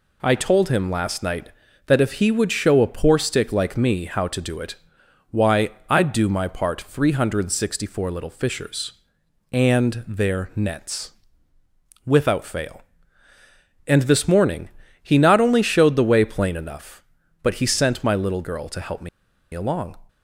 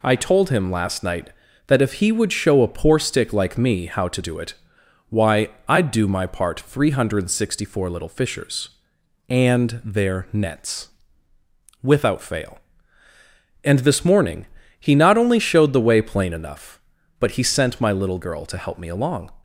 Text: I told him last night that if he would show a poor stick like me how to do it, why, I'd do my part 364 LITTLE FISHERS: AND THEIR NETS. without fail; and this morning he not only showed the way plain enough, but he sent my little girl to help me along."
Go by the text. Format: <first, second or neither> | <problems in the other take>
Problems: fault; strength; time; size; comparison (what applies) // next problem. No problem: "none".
second | pauses between "morning" and "he"; slight; at 14.6 s; 0.34 s long; slight in the second // pauses between "me" and "along"; at 19.0 s; 0.45 s long